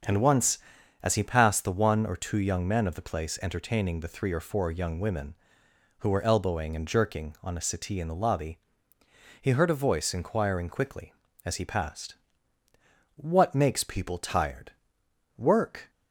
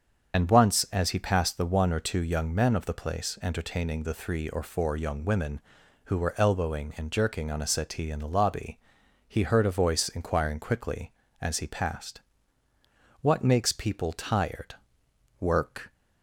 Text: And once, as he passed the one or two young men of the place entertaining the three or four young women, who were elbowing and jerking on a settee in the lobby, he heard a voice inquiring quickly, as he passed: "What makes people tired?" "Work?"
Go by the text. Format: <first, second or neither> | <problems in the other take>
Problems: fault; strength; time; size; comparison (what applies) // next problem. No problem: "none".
first | loses the start of "And"; at 0.3 s; 55 ms // starts louder than the rest; strong; until 1.4 s; 7.5 dB; also in the first